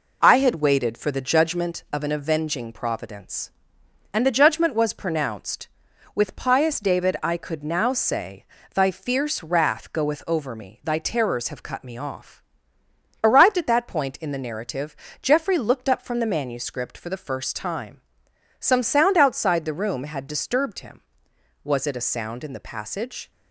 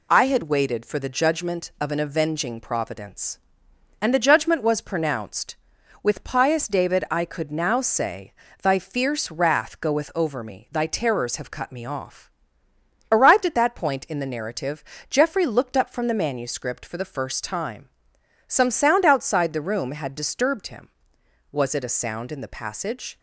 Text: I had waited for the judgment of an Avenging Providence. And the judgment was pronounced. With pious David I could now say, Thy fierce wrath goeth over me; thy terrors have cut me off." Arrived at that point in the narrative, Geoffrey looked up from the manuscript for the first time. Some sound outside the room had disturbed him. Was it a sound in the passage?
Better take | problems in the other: second | starts louder than the rest; until 1.8 s; 4 dB

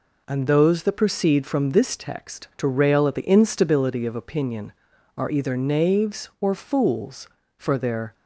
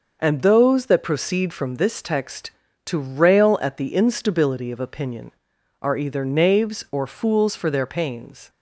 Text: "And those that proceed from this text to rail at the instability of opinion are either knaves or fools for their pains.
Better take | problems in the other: second | stops before "pains"; at 8.1 s

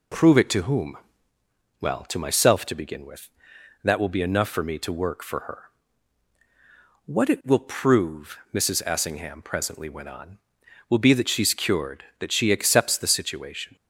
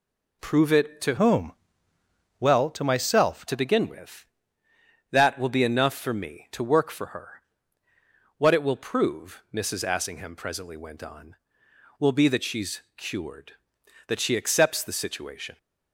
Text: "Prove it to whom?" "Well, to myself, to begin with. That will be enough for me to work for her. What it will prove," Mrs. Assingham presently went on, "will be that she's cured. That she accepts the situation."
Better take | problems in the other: first | changes voice from "whom" to "myself"; from 1.1 to 3.4 s; 2.3 s long // pauses between "she's" and "cured"; slight; at 12.7 s; 0.16 s long

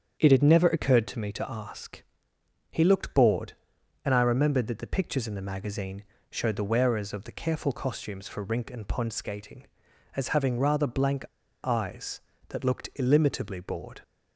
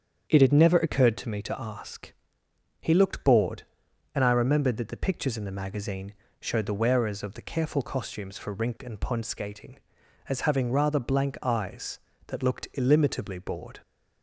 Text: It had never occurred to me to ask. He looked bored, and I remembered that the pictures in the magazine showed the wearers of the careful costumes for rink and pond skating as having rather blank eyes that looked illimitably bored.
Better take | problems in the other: second | starts louder than the rest; strong; until 1.2 s; 8 dB; strong in the second // pauses between "magazine" and "showed"; slight; at 6.0 s; 0.26 s long; slight in the second // pauses between "blank" and "eyes"; at 11.2 s; 0.40 s long

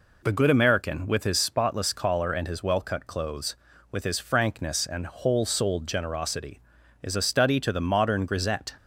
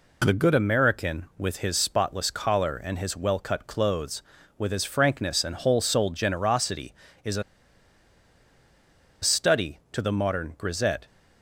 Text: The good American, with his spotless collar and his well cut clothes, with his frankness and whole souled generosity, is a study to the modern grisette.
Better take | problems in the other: first | pauses between "a" and "study"; strong; at 7.4 s; 1.7 s long

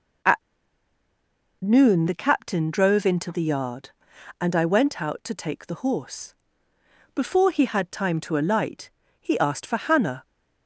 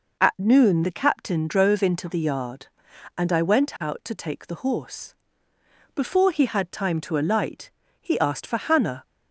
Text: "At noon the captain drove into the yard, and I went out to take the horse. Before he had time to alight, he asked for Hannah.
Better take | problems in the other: second | pauses between "At" and "noon"; at 0.3 s; 1.2 s long

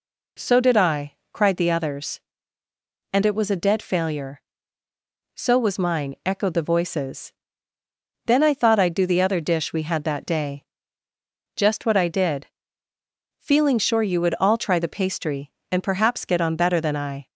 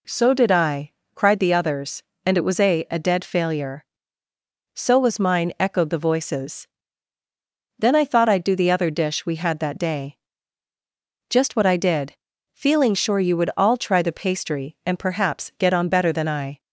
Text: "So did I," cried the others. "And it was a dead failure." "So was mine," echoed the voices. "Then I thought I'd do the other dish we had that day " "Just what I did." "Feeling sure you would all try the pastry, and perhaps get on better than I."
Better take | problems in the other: first | says "a" twice; at 2.9 s

